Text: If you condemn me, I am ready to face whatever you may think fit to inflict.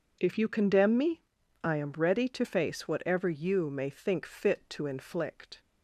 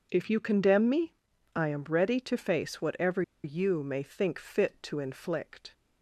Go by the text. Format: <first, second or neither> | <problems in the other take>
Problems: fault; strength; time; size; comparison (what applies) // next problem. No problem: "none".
first | pauses between "whatever" and "you"; slight; at 3.2 s; 0.22 s long